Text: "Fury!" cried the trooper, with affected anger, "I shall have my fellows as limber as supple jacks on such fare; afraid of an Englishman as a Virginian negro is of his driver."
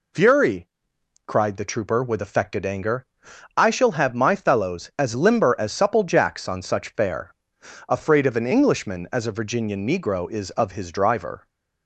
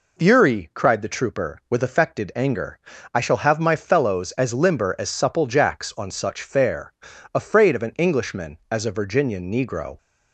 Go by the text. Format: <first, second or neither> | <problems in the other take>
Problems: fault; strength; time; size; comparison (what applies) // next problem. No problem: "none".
first | stops before "is of his driver"; at 9.9 s